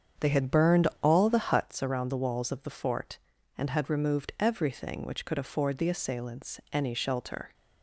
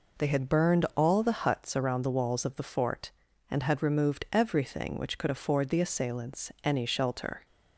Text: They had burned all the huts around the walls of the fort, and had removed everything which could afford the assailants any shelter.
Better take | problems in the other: second | starts louder than the rest; strong; until 1.7 s; 7.5 dB

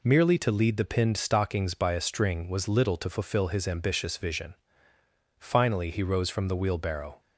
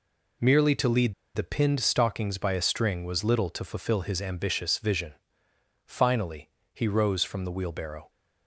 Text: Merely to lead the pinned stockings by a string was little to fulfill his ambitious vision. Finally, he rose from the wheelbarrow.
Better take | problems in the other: first | pauses between "lead" and "the"; slight; at 1.1 s; 0.21 s long

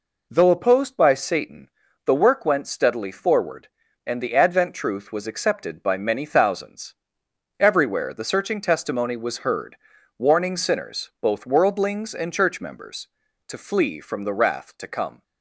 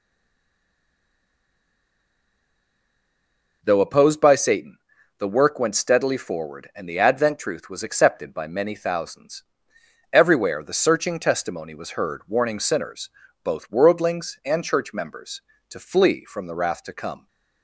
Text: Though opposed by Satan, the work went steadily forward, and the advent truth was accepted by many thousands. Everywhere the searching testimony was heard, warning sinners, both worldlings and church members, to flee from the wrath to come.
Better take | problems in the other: first | stays silent before the first word; strong; until 3.6 s; 3.6 s long

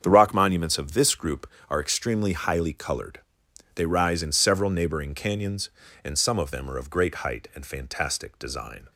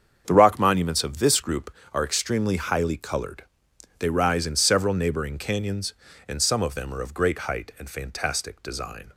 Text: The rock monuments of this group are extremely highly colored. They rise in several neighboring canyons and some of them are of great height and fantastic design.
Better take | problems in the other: neither | starts louder than the rest; strong; the same in both

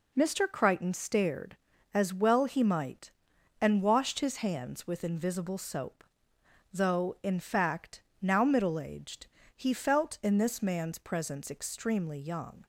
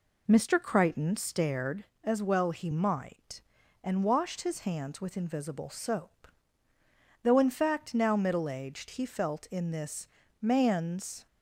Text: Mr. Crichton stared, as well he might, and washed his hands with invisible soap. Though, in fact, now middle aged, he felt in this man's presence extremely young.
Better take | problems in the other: first | pauses between "this" and "man's"; slight; at 10.0 s; 0.32 s long // stops before "presence extremely young"; at 11.2 s

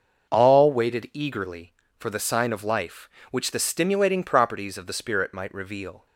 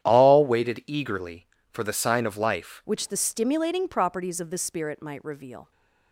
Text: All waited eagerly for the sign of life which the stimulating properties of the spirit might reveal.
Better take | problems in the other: first | starts louder than the rest; strong; until 1.0 s; 10.5 dB // changes voice at "which"; from 2.8 s on; 2.9 s long

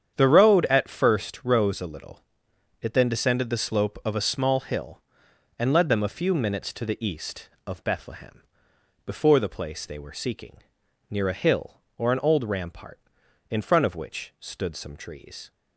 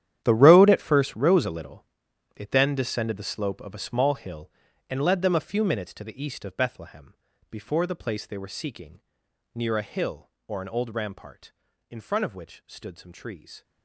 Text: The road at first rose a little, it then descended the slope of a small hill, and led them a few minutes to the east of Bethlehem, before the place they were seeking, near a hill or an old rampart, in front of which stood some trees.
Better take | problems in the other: first | gets quieter; strong; throughout; 15 dB // starts louder than the rest; strong; until 1.2 s; 11 dB; strong in the first

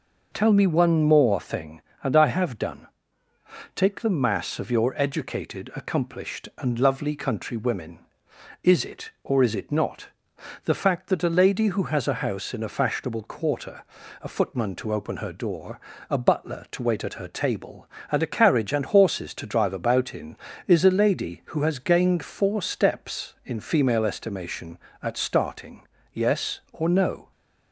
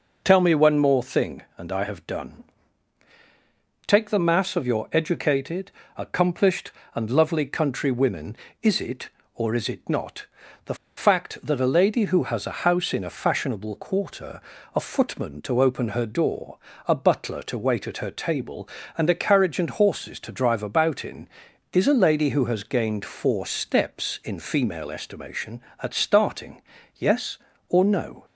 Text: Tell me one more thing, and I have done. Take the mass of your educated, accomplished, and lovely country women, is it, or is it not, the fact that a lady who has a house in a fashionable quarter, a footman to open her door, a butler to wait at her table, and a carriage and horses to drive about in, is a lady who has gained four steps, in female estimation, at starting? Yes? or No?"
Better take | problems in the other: first | pauses between "the" and "fact"; slight; at 10.7 s; 0.21 s long

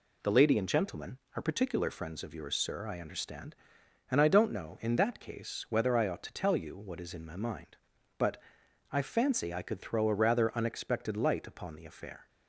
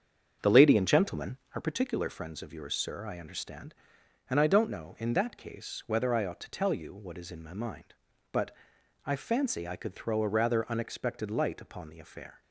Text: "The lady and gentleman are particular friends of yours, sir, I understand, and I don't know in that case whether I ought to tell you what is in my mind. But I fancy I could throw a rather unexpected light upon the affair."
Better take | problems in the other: first | starts louder than the rest; strong; until 1.6 s; 7.5 dB // pauses between "But" and "I"; noticeable; at 8.5 s; 0.48 s long; noticeable in the first

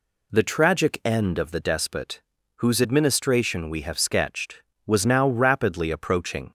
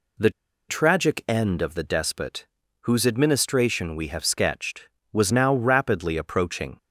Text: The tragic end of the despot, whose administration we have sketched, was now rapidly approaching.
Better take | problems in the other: first | pauses between "The" and "tragic"; at 0.3 s; 0.37 s long

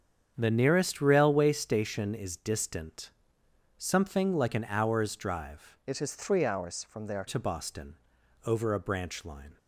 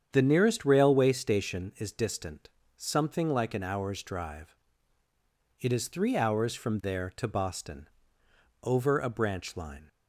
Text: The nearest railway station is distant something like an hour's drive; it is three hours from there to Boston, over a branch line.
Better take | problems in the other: second | starts louder than the rest; strong; until 1.3 s; 7.5 dB; strong in the second // pauses between "distant" and "something"; noticeable; at 3.1 s; 0.68 s long; slight in the second // changes voice from "it" to "there"; from 5.8 to 7.2 s; 1.4 s long

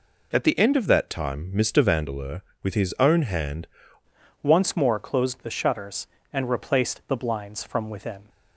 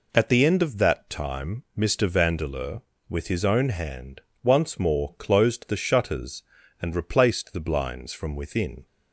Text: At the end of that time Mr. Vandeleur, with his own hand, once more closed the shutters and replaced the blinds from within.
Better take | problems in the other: second | changes voice at "once"; from 4.4 s on; 3.8 s long

